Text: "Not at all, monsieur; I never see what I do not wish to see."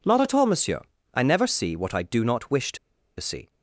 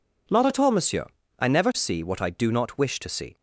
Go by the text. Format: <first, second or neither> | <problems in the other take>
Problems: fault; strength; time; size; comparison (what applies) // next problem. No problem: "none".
second | pauses between "to" and "see"; at 2.7 s; 0.42 s long